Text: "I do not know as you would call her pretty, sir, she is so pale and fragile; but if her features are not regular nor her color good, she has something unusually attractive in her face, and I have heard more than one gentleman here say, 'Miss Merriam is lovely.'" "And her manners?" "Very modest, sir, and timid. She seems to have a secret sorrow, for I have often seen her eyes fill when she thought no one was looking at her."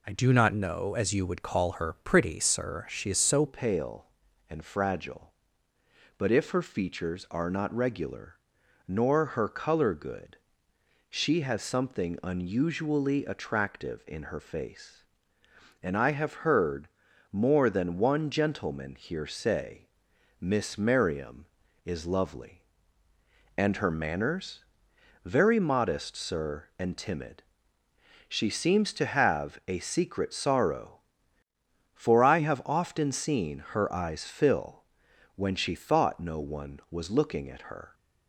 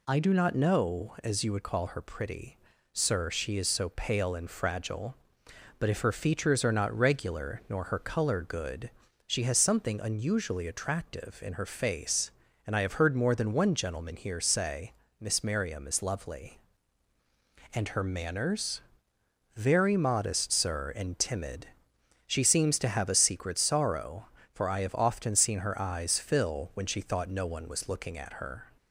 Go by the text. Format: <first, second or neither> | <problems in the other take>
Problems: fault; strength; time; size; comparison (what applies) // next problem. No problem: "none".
second | changes voice at "pale"; from 3.4 s on; 34.5 s long // pauses between "regular" and "nor"; noticeable; at 8.3 s; 0.50 s long // pauses between "heard" and "more"; at 16.8 s; 0.44 s long // pauses between "fill" and "when"; noticeable; at 34.8 s; 0.52 s long